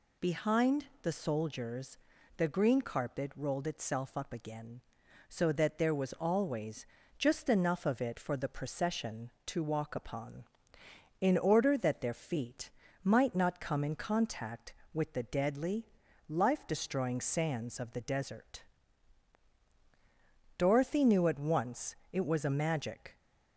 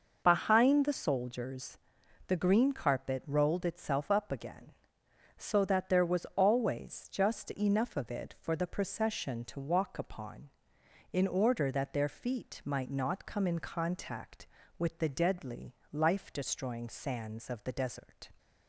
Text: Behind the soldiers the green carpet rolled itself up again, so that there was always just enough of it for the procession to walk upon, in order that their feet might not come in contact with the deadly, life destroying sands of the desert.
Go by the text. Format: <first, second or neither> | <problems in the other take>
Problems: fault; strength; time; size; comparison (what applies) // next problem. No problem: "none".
second | pauses between "Behind" and "the"; slight; at 0.8 s; 0.18 s long // pauses between "soldiers" and "the"; at 1.9 s; 0.42 s long; noticeable in the second // pauses between "always" and "just"; slight; at 6.8 s; 0.32 s long // pauses between "feet" and "might"; slight; at 12.6 s; 0.32 s long // goes on to say "Dorothy knew at once it was a magic"; strong; from 20.5 s on; 2.6 s long